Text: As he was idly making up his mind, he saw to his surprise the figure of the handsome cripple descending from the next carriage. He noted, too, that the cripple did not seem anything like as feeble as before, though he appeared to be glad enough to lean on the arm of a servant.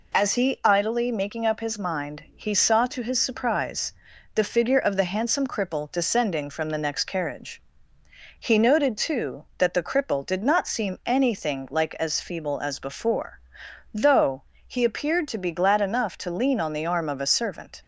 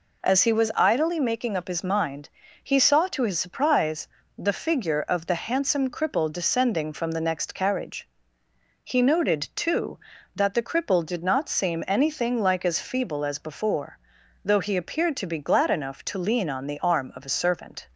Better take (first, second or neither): second